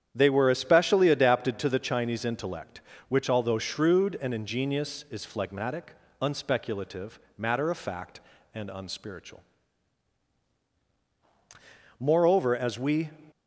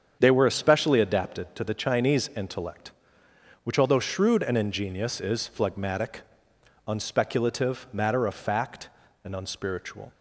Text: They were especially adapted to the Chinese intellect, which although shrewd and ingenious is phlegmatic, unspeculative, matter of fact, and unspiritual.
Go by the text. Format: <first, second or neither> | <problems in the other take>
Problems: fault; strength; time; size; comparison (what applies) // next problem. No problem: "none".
second | starts louder than the rest; strong; until 1.1 s; 9 dB; strong in the second // goes on to say "Moreover as we"; noticeable; from 11.9 s on; 1.1 s long